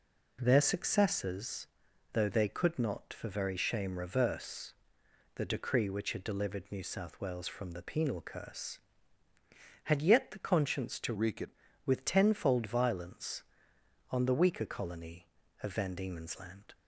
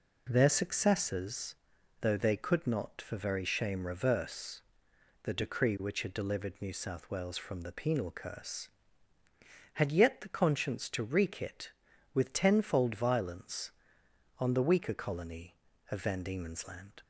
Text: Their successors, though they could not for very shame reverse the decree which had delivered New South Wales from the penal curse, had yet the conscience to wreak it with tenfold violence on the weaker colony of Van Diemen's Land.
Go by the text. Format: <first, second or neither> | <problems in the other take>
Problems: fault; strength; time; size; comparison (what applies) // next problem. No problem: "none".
second | pauses between "reverse" and "the"; noticeable; at 4.7 s; 0.62 s long; noticeable in the second // changes voice from "wreak" to "it"; from 11.1 to 11.5 s; 0.4 s long